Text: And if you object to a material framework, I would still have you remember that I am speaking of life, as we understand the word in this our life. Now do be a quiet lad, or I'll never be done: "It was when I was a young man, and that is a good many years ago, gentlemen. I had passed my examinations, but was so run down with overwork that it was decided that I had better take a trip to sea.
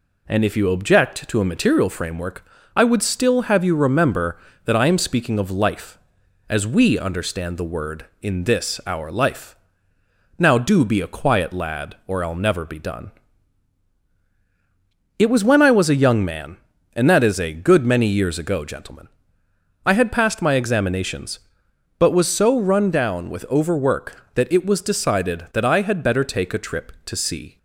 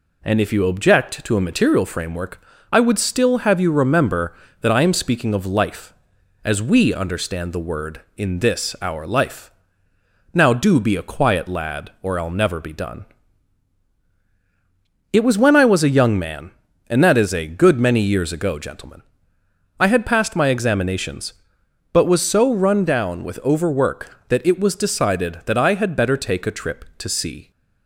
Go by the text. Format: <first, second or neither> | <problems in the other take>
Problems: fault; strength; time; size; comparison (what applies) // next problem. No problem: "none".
neither | none